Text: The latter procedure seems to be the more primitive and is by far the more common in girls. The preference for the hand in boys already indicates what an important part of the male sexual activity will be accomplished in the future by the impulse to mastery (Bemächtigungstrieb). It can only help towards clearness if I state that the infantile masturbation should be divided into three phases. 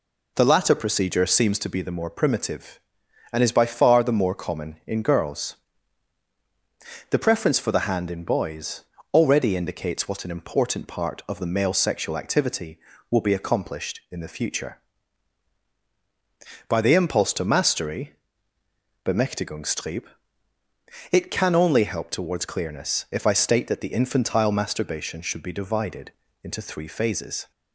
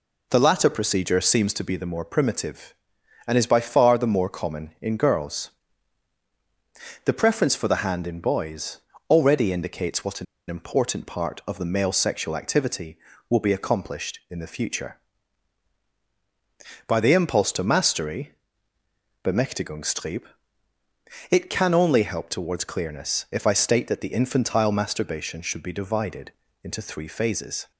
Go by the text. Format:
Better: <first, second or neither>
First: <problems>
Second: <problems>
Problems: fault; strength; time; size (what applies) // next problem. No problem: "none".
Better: first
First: pauses between "boys" and "already"; slight; at 8.8 s; 0.28 s long // pauses between "divided" and "into"; slight; at 26.1 s; 0.28 s long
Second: pauses between "boys" and "already"; slight; at 8.8 s; 0.28 s long // pauses between "an" and "important"; slight; at 10.2 s; 0.23 s long // pauses between "divided" and "into"; slight; at 26.3 s; 0.28 s long